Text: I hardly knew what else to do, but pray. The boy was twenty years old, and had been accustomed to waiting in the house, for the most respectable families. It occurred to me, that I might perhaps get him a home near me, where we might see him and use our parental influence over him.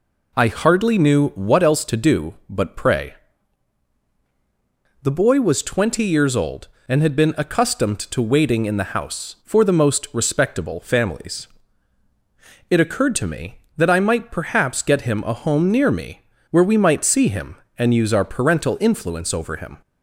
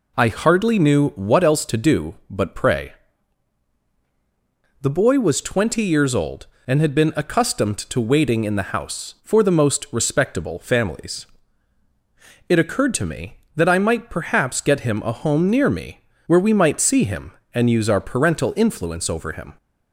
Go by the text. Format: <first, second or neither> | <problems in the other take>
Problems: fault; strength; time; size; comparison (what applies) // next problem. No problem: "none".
neither | none